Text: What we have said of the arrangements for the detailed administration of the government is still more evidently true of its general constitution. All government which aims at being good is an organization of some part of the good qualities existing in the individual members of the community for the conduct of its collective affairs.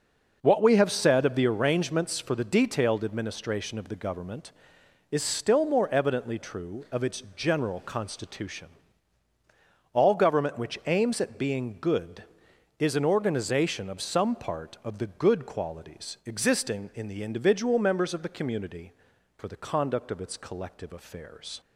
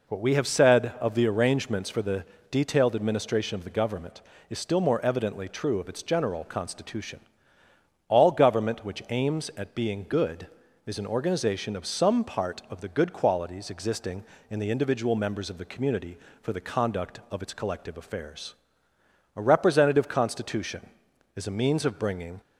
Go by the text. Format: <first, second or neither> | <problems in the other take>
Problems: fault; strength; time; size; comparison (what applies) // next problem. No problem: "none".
first | pauses between "the" and "detailed"; slight; at 2.2 s; 0.26 s long // goes on to say "A representative constitution is a means of bringing"; strong; from 19.3 s on; 3.0 s long